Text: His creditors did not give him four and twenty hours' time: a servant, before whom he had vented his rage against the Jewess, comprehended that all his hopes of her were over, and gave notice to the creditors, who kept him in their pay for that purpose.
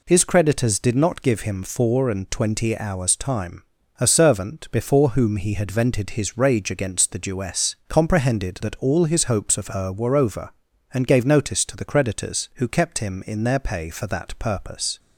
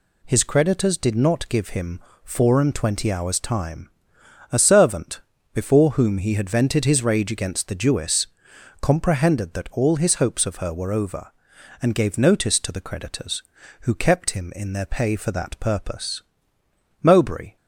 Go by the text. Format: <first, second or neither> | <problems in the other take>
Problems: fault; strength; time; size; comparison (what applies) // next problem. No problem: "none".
first | pauses between "him" and "four"; slight; at 2.0 s; 0.24 s long // goes on to say "Mowbray"; from 17.0 s on; 0.54 s long